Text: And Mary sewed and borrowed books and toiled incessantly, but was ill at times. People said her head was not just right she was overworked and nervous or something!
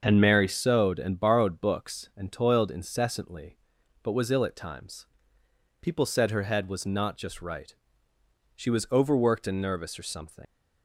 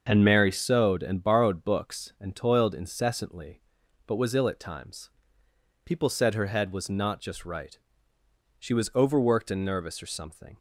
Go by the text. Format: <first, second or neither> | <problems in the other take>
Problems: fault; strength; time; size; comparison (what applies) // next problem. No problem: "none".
second | starts louder than the rest; until 1.0 s; 6.5 dB; also in the second // pauses between "right" and "she"; noticeable; at 7.7 s; 0.82 s long; noticeable in the second // leaves "something" unfinished; at 10.4 s; 85 ms